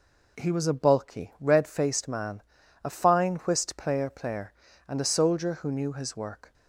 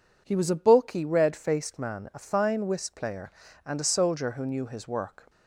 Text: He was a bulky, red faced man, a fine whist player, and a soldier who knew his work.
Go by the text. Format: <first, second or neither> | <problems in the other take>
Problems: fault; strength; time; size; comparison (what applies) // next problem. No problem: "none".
second | says "player" twice; at 4.0 s